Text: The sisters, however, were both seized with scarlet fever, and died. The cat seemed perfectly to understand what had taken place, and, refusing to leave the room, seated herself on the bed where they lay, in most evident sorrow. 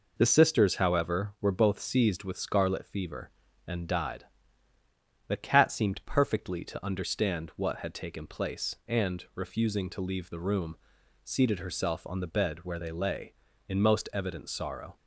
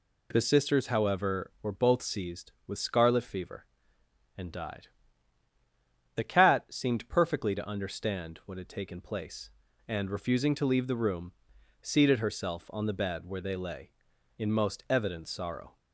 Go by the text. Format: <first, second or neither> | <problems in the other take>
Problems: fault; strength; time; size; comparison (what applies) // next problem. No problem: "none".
neither | none